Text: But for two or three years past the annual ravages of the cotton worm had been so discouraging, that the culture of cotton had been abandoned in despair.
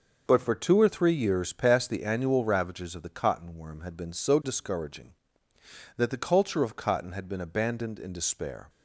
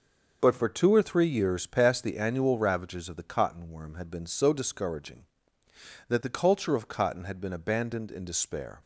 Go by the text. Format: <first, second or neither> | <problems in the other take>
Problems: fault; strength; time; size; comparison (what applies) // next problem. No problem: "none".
neither | none